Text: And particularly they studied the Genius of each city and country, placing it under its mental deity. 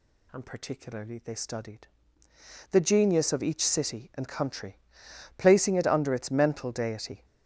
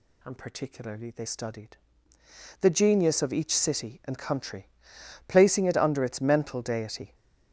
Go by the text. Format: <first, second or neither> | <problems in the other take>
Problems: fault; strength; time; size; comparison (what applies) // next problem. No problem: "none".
neither | pauses between "studied" and "the"; noticeable; the same in both